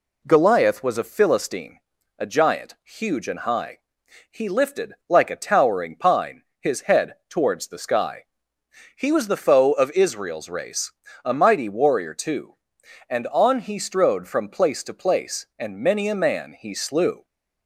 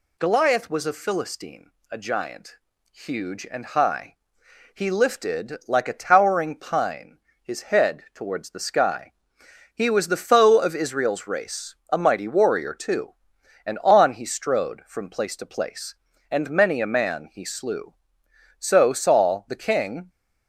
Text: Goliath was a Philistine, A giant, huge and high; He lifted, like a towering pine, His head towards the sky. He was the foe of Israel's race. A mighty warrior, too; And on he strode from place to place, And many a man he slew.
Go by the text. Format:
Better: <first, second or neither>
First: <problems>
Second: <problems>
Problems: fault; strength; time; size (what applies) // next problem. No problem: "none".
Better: first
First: none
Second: goes on to say "So Saul the king"; from 18.5 s on; 1.5 s long